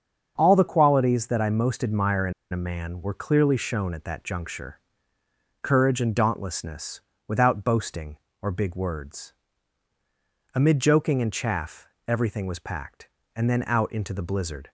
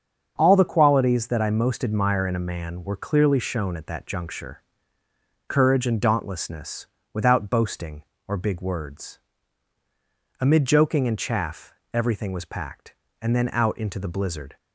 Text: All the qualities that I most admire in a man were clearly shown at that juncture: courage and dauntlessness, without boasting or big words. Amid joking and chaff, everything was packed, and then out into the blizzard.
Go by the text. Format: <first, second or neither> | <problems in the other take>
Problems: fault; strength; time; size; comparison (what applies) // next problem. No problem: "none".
second | starts louder than the rest; until 1.3 s; 7 dB; also in the second // pauses between "in" and "a"; slight; at 2.3 s; 0.19 s long